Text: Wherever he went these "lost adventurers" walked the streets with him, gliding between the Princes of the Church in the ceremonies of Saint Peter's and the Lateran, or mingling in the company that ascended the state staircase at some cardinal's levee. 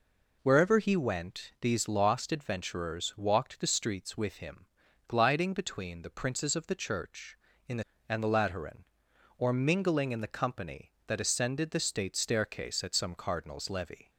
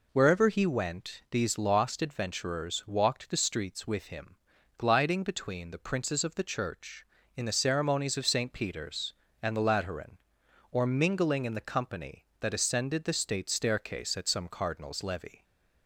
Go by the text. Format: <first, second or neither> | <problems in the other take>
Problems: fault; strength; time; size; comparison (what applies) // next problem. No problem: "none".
second | skips "ceremonies of Saint Peter's"; at 7.9 s